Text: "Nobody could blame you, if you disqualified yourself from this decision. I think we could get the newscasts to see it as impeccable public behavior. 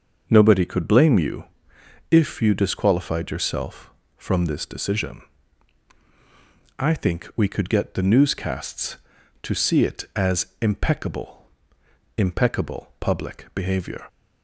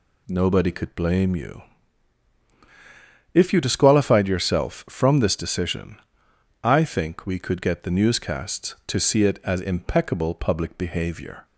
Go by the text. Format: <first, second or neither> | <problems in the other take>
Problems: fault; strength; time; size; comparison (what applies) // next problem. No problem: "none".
second | starts louder than the rest; until 1.2 s; 6 dB // says "impeccable" twice; at 12.1 s